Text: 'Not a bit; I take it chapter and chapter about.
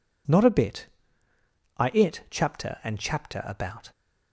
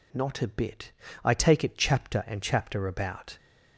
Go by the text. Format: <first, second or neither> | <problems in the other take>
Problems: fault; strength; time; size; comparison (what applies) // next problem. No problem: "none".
second | skips "take"; at 1.9 s